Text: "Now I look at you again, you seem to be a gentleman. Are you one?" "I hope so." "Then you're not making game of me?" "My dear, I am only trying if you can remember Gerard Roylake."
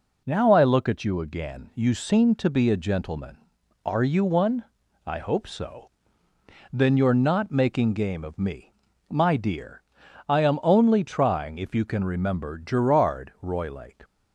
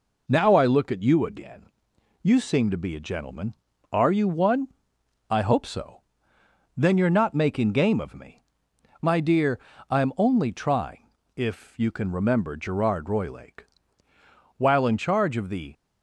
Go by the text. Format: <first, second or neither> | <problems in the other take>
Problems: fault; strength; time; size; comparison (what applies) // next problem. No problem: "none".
first | pauses between "trying" and "if"; slight; at 11.1 s; 0.26 s long // goes on to say "While in charge of the"; noticeable; from 14.5 s on; 1.1 s long